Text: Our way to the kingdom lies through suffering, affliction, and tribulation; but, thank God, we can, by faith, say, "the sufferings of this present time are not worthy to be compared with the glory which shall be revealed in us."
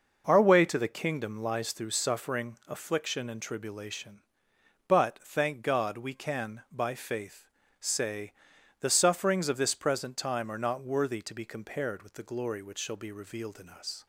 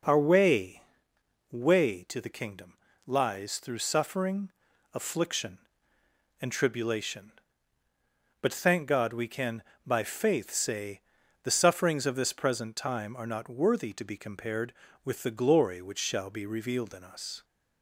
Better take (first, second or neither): first